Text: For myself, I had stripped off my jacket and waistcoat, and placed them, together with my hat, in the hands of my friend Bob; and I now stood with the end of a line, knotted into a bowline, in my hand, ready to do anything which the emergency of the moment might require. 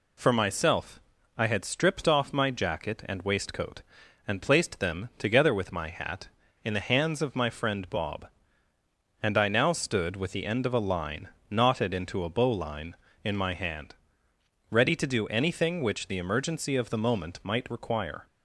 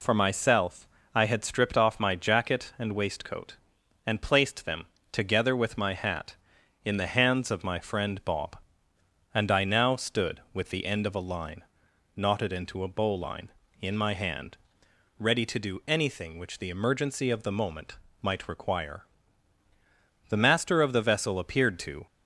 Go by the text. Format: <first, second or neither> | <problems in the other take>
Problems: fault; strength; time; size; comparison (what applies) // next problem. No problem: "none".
first | pauses between "moment" and "might"; slight; at 17.9 s; 0.24 s long // goes on to say "The master of the vessel appeared to"; strong; from 20.2 s on; 1.7 s long